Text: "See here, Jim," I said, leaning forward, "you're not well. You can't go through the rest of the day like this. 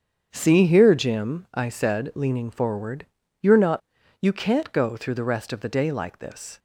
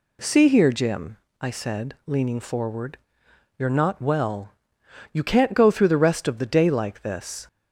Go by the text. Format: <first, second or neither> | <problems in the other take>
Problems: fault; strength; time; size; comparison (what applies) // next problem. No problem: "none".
second | starts louder than the rest; strong; until 1.3 s; 7.5 dB // skips "well"; at 4.0 s